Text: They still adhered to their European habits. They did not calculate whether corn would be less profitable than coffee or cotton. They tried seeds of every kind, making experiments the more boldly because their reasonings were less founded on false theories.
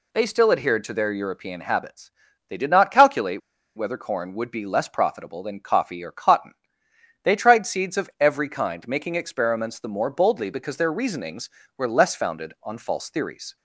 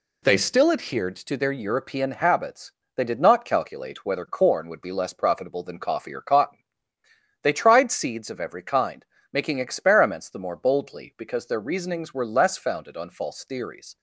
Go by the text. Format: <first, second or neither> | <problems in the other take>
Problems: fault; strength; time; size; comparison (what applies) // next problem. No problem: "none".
second | pauses between "calculate" and "whether"; slight; at 3.4 s; 0.35 s long